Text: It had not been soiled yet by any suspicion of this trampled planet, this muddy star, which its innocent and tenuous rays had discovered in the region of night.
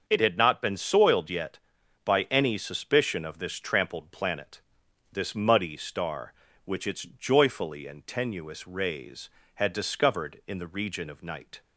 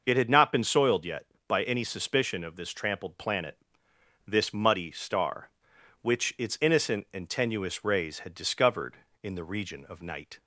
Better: second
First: starts louder than the rest; until 1.0 s; 6.5 dB // says "joyfully" for "innocent"; at 7.0 s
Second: starts louder than the rest; noticeable; until 1.0 s; 6 dB

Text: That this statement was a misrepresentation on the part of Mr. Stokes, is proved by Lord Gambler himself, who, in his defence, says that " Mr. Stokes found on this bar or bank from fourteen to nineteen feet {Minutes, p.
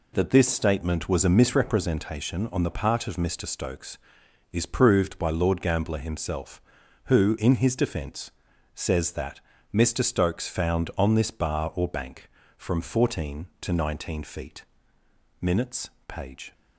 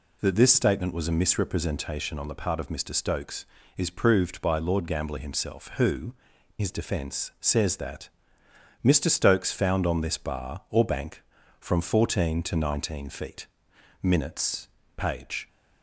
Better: first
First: none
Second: skips "in"; at 6.3 s

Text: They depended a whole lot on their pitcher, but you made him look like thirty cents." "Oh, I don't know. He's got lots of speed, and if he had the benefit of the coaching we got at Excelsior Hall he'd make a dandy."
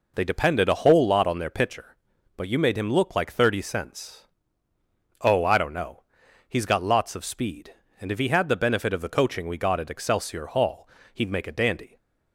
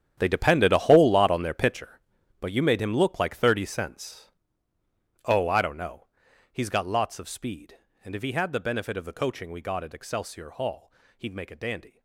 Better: first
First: pauses between "Hall" and "he'd"; slight; at 10.8 s; 0.26 s long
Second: gets quieter; strong; throughout; 15.5 dB // pauses between "Hall" and "he'd"; slight; at 10.9 s; 0.26 s long

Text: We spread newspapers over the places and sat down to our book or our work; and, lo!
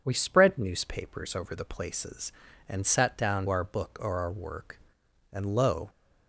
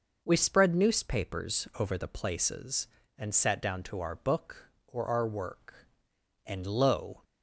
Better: second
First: skips "to"; at 3.4 s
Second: none

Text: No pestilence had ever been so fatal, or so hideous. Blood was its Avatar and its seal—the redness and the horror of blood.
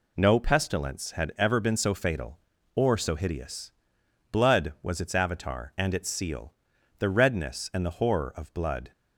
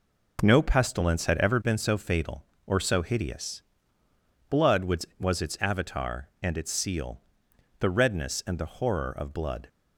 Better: first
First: none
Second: says "was" twice; at 5.1 s

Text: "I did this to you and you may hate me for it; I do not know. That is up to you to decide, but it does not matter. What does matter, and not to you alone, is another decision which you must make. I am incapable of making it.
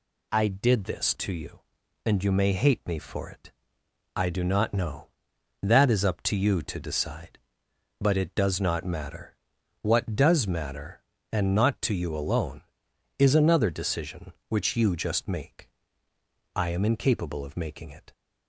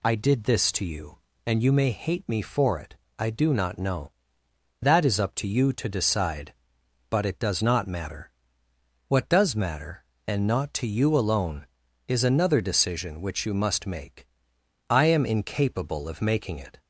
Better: second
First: says "just" for "must"; at 14.9 s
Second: none

